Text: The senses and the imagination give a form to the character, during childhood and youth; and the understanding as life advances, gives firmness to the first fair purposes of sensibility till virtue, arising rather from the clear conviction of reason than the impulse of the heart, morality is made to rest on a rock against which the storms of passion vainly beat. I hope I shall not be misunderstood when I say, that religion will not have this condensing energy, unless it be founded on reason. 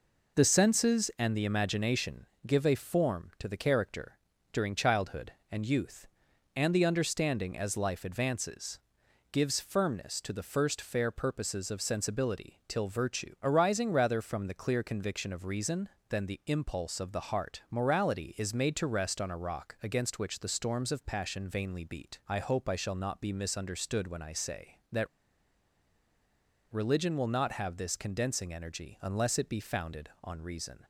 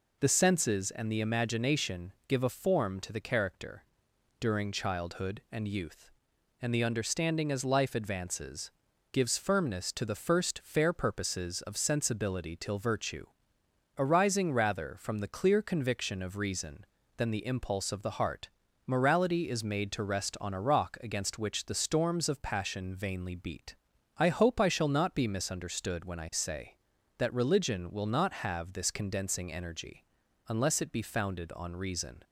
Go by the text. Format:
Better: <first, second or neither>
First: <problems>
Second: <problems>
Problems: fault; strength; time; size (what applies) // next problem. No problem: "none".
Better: second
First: pauses between "imagination" and "give"; slight; at 2.2 s; 0.18 s long // pauses between "that" and "religion"; strong; at 25.0 s; 1.6 s long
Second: none